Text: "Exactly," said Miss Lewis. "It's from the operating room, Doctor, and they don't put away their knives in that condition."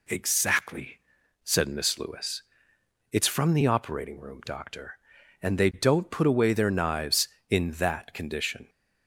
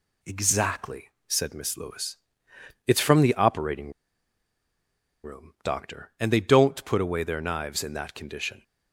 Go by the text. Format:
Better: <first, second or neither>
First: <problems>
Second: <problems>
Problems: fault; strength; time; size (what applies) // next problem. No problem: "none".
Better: first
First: none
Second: pauses between "operating" and "room"; strong; at 3.8 s; 1.3 s long